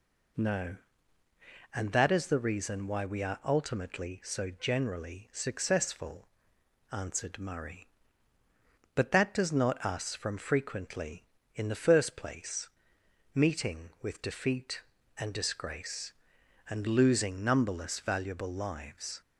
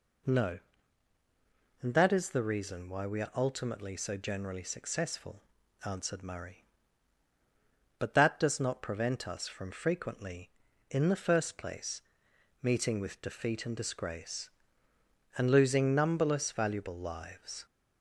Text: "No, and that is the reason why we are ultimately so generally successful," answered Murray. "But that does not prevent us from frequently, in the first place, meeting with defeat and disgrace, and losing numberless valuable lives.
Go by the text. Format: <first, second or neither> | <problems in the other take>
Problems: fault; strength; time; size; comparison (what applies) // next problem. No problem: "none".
second | skips "prevent"; at 9.8 s